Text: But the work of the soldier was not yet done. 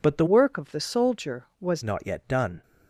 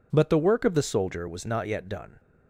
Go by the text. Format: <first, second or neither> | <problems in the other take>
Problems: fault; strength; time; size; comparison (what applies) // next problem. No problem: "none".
second | changes voice from "work" to "was"; from 0.2 to 1.8 s; 1.6 s long